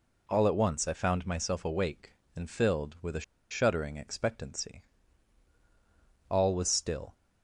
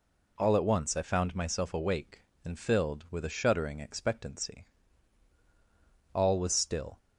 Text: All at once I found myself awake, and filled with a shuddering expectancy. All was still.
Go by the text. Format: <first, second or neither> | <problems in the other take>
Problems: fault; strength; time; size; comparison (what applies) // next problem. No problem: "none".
second | pauses between "a" and "shuddering"; slight; at 3.2 s; 0.28 s long